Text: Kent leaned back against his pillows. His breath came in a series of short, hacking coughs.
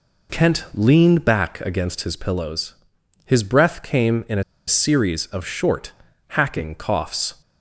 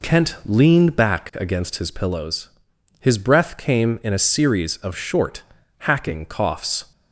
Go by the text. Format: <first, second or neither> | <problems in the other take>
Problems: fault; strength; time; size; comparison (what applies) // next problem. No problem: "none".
second | pauses between "a" and "series"; slight; at 4.4 s; 0.25 s long